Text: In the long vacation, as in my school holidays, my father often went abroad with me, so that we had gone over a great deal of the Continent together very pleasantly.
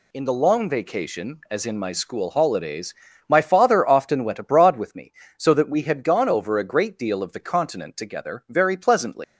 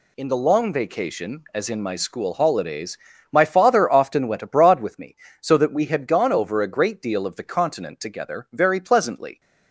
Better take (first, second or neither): second